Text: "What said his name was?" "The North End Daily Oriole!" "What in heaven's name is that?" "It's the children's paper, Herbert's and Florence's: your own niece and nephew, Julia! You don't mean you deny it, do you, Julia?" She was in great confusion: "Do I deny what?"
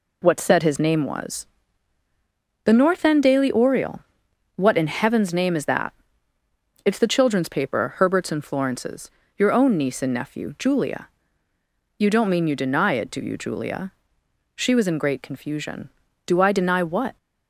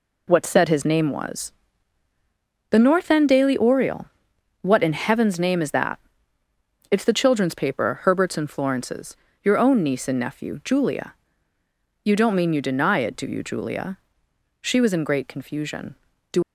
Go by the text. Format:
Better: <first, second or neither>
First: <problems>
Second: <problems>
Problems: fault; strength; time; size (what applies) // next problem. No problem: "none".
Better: first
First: none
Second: stops before "I deny what"; at 16.4 s